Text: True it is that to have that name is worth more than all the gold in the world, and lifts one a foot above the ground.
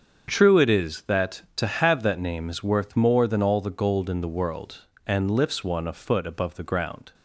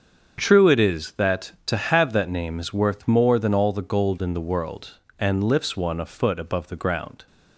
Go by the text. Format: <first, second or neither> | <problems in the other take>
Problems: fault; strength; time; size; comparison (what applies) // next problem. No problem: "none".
neither | starts louder than the rest; strong; the same in both